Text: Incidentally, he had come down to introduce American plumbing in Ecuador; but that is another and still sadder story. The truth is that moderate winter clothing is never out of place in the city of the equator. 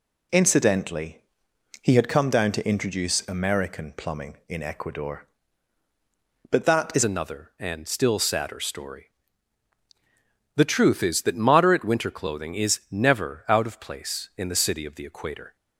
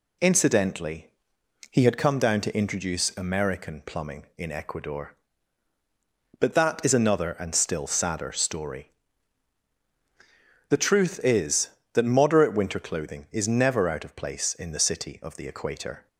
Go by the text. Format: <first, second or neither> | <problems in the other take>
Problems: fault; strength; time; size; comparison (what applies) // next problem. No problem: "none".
second | changes voice at "another"; from 7.0 s on; 8.5 s long